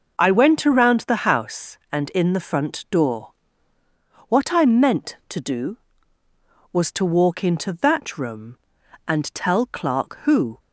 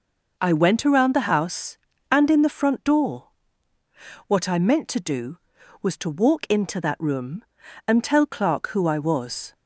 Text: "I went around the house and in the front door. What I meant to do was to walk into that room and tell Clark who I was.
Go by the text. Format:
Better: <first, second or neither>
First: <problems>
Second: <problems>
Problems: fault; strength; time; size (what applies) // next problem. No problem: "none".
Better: second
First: stops before "I was"; at 10.5 s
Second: none